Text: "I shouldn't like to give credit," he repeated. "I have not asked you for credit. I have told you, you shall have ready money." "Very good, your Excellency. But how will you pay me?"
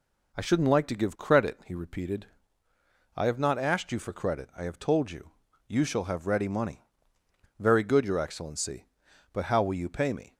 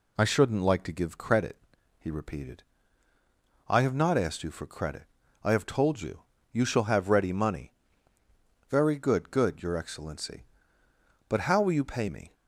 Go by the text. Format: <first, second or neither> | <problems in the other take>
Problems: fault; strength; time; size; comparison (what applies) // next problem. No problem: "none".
first | says "good" twice; at 9.2 s